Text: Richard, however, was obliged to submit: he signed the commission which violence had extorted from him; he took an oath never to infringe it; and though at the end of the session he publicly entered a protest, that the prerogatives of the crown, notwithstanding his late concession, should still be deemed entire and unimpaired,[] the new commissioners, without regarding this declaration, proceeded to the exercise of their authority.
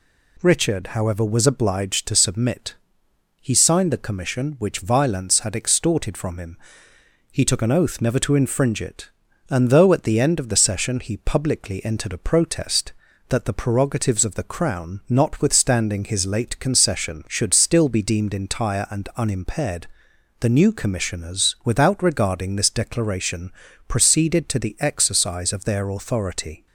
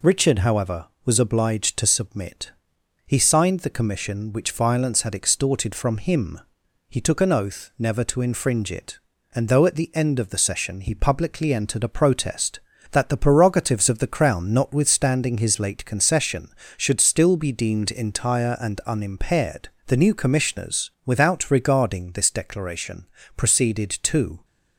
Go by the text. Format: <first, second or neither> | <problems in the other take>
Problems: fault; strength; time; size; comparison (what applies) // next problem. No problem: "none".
first | stops before "the exercise of their authority"; at 24.4 s